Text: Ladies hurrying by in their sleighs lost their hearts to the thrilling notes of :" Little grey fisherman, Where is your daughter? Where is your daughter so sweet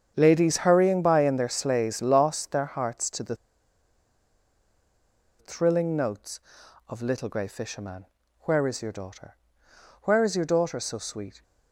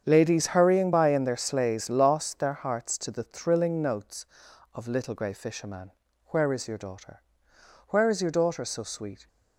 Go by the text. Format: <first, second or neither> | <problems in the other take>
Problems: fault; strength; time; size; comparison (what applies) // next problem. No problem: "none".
second | starts louder than the rest; strong; until 1.1 s; 7.5 dB; strong in the second // pauses between "the" and "thrilling"; strong; at 3.3 s; 2.0 s long